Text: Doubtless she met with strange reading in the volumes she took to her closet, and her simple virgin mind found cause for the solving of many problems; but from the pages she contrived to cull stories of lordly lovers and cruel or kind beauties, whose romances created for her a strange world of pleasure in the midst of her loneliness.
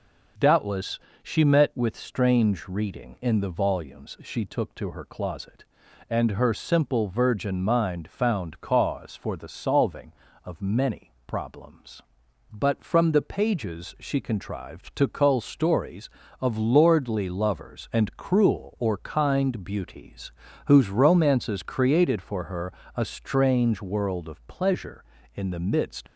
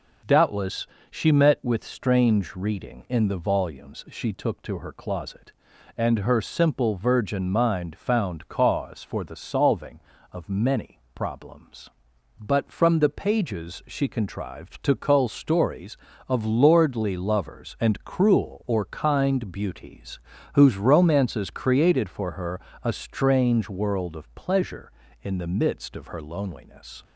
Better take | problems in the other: second | pauses between "Doubtless" and "she"; slight; at 0.9 s; 0.24 s long; slight in the second // pauses between "her" and "a"; slight; at 22.7 s; 0.20 s long; slight in the second // stops before "of her loneliness"; at 26.0 s

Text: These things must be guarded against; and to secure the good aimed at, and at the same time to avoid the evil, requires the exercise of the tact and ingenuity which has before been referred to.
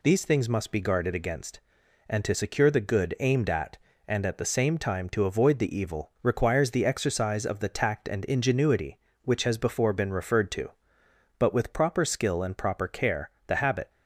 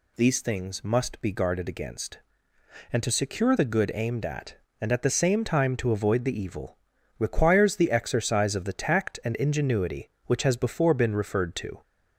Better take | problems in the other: second | goes on to say "But with proper skill and proper care the habit"; strong; from 11.3 s on; 2.5 s long

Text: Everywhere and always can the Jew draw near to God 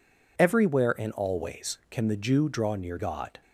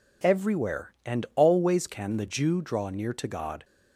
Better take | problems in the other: second | skips "to"; at 2.9 s

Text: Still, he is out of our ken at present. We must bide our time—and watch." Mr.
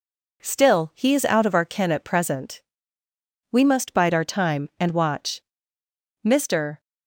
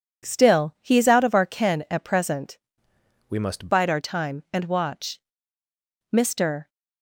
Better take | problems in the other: first | changes voice from "We" to "must"; from 3.2 to 3.6 s; 0.4 s long

